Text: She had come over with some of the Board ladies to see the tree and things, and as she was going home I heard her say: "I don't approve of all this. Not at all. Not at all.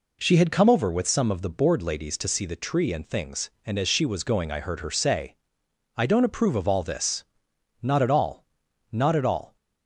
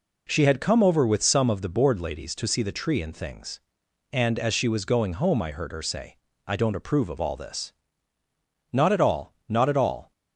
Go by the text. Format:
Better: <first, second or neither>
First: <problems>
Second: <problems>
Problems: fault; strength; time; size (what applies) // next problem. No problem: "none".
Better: second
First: skips "home"; at 4.5 s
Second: none